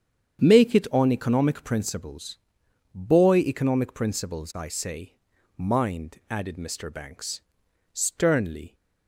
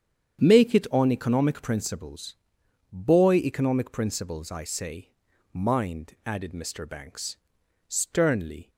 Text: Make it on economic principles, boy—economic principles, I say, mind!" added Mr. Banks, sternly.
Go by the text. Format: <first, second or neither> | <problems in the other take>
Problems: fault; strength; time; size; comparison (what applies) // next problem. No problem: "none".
neither | starts louder than the rest; strong; the same in both